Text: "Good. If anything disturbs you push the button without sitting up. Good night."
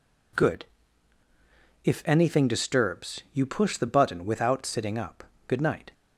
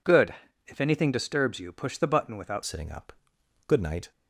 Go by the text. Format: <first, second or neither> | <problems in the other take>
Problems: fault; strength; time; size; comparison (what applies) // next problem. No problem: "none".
first | changes voice at "sitting"; from 2.6 s on; 1.5 s long